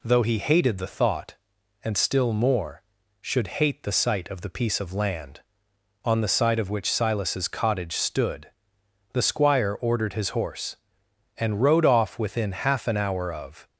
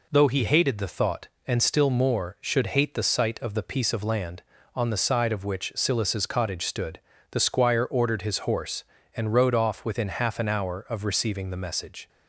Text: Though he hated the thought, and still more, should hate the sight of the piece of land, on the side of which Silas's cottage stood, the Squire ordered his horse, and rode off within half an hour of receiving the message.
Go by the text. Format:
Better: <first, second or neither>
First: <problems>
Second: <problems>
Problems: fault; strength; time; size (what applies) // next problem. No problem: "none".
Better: second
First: stops before "receiving the message"; at 13.6 s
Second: none